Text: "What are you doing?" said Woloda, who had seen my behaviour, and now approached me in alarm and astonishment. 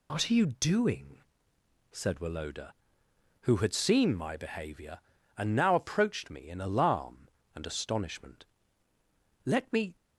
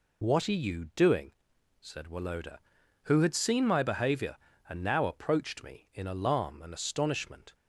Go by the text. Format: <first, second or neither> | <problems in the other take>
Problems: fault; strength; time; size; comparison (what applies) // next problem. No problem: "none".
second | goes on to say "Let me"; from 9.4 s on; 0.50 s long